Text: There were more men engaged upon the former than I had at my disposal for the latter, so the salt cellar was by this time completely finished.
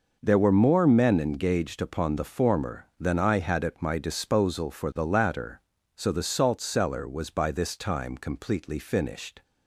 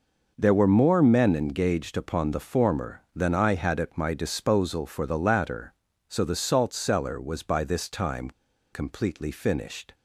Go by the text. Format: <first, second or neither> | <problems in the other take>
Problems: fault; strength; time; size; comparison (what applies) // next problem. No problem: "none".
first | pauses between "time" and "completely"; at 8.2 s; 0.42 s long